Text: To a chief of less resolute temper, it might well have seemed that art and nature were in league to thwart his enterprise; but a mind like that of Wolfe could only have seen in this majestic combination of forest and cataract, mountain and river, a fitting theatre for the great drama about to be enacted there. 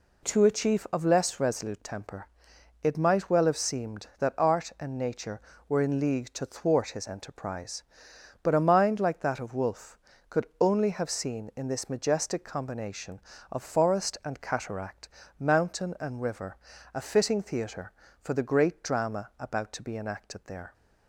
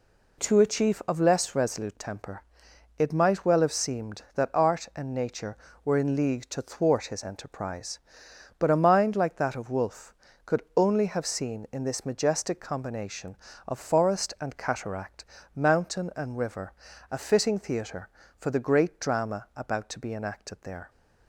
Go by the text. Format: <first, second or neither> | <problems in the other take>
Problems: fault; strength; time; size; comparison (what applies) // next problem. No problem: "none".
neither | none